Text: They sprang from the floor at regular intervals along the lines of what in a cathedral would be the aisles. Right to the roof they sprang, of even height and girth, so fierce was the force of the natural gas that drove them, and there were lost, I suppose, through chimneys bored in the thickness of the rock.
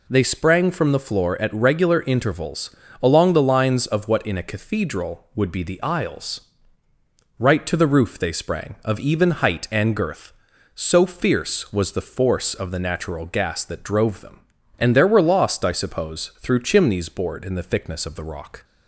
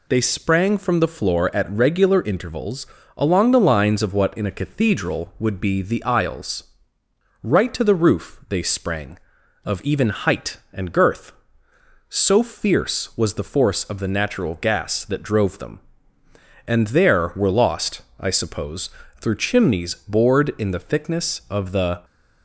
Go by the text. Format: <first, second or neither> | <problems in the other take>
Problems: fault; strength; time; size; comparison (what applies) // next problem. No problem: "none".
first | pauses between "intervals" and "along"; slight; at 2.8 s; 0.30 s long; slight in the first // stops before "rock"; at 22.0 s